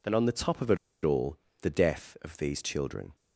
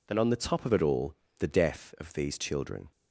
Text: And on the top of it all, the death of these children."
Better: second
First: pauses between "it" and "all"; slight; at 0.7 s; 0.27 s long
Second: none

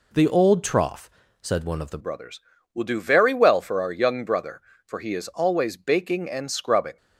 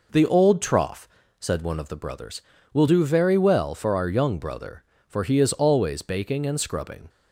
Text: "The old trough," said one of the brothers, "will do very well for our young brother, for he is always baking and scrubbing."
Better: second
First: changes voice at "brothers"; from 1.9 s on; 5.0 s long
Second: none

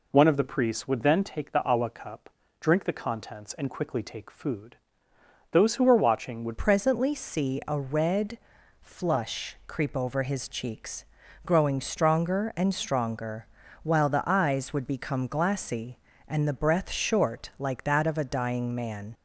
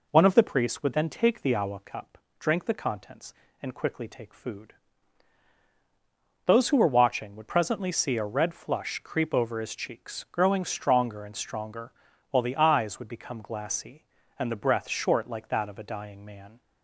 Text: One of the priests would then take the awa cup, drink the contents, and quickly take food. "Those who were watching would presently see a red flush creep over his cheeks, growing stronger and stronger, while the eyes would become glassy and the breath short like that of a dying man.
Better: second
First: changes voice at "presently"; from 6.5 s on; 12.6 s long // pauses between "red" and "flush"; at 8.3 s; 0.42 s long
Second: none

